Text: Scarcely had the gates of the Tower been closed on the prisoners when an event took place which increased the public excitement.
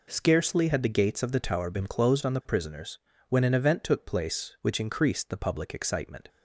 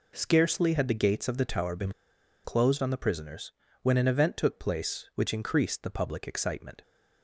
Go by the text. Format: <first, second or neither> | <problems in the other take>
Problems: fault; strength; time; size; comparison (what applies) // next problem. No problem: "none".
first | pauses between "been" and "closed"; noticeable; at 1.9 s; 0.54 s long // pauses between "prisoners" and "when"; slight; at 3.5 s; 0.32 s long; slight in the first